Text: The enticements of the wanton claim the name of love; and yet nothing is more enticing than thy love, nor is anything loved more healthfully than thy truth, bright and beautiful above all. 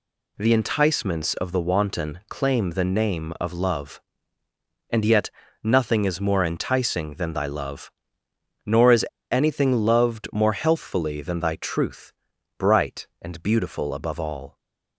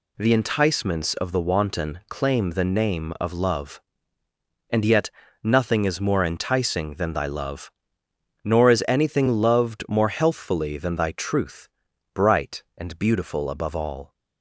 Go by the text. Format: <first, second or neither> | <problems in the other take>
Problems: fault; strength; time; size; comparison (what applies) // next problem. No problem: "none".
second | pauses between "yet" and "nothing"; slight; at 5.2 s; 0.34 s long; slight in the second // pauses between "is" and "anything"; slight; at 9.0 s; 0.26 s long